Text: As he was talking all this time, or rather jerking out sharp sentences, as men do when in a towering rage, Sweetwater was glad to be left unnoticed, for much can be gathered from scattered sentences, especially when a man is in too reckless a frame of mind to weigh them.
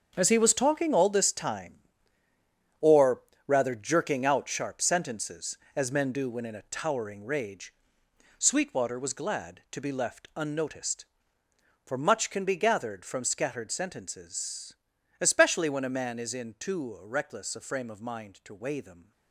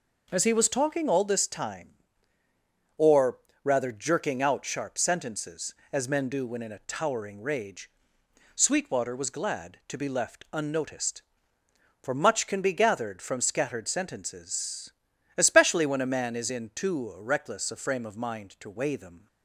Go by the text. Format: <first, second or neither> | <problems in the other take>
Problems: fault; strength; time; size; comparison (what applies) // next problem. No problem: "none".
second | gets quieter; strong; throughout; 11 dB // pauses between "or" and "rather"; slight; at 3.2 s; 0.26 s long; slight in the second